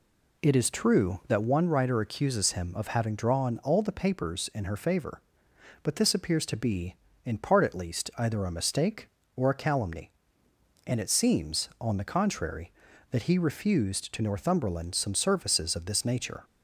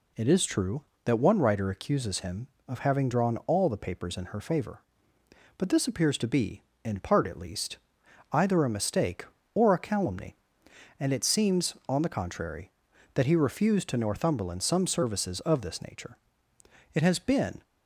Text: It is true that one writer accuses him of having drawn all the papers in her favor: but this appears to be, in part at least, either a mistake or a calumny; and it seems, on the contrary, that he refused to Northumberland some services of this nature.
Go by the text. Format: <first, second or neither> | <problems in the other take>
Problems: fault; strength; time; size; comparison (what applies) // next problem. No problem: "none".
first | goes on to say "It has been"; noticeable; from 16.9 s on; 0.70 s long